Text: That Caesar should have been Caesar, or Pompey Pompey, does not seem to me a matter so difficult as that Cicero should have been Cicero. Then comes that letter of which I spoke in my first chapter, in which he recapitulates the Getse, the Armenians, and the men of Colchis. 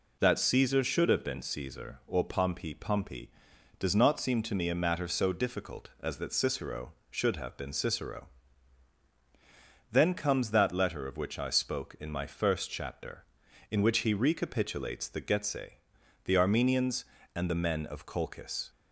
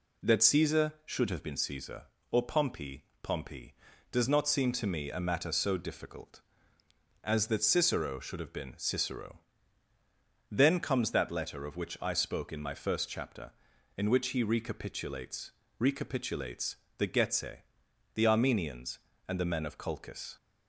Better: first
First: none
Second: pauses between "Pompey" and "Pompey"; slight; at 3.0 s; 0.18 s long // says "recapitulates" twice; at 15.7 s

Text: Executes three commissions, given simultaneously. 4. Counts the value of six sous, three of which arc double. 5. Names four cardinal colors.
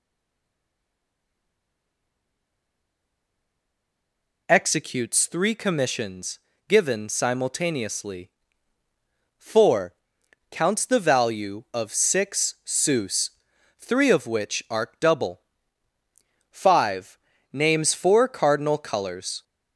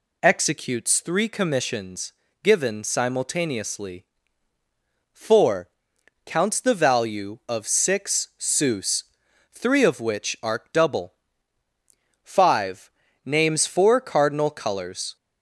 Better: second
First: stays silent before the first word; strong; until 4.4 s; 4.4 s long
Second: none

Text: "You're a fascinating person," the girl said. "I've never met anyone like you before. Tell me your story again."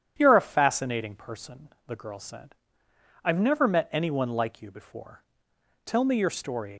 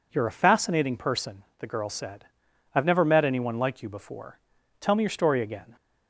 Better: second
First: starts louder than the rest; strong; until 1.1 s; 9.5 dB // stops before "again"; at 6.7 s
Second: none

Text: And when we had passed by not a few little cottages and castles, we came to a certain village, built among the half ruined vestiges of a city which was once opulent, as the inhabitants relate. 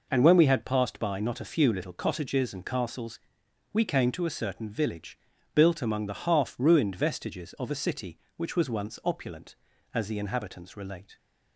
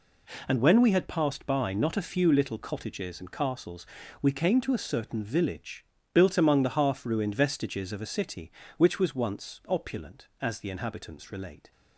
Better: neither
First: none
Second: none

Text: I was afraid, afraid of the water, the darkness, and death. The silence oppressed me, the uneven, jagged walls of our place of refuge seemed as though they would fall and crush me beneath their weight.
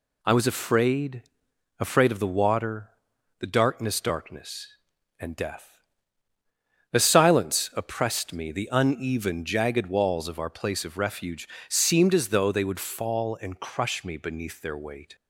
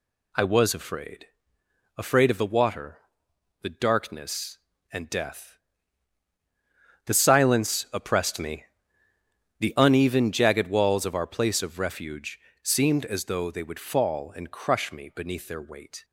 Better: second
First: says "darkness" twice; at 3.9 s // pauses between "refuge" and "seemed"; slight; at 11.4 s; 0.22 s long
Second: pauses between "refuge" and "seemed"; slight; at 12.3 s; 0.24 s long

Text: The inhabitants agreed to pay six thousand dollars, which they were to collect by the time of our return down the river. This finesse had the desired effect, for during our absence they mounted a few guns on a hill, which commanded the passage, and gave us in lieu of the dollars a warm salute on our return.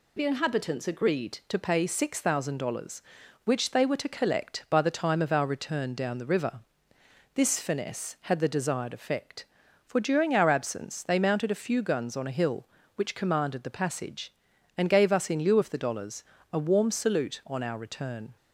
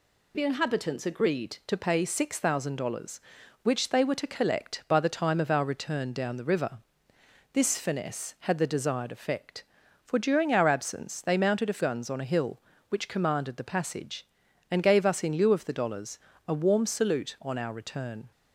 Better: first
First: pauses between "dollars" and "a"; slight; at 16.2 s; 0.26 s long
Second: skips "few"; at 11.8 s // pauses between "dollars" and "a"; slight; at 16.1 s; 0.26 s long

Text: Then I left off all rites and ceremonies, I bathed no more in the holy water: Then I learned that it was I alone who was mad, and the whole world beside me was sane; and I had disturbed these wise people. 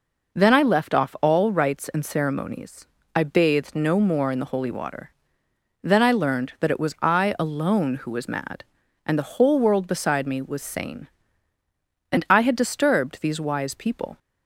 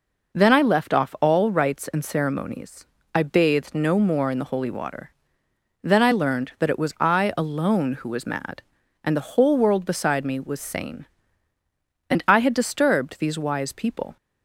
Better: neither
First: none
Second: none

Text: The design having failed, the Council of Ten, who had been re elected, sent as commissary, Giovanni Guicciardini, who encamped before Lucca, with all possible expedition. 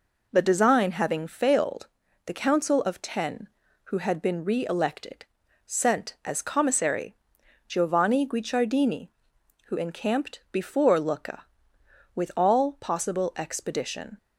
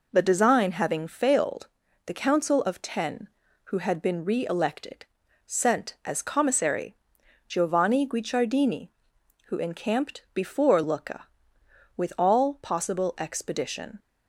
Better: neither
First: none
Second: none

